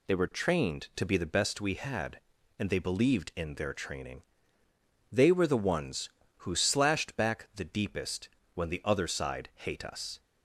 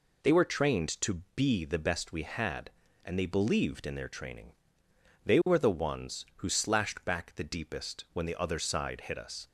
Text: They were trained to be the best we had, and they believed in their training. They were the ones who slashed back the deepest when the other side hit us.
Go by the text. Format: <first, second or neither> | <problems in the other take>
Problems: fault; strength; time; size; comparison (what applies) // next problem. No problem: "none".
second | pauses between "deepest" and "when"; slight; at 8.2 s; 0.24 s long // says "hate" for "hit"; at 9.5 s